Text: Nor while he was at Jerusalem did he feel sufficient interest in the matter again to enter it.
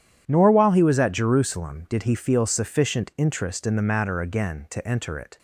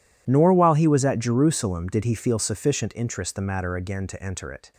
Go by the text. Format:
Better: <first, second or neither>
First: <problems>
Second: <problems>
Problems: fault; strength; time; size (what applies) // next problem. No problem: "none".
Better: first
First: none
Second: skips "in"; at 3.3 s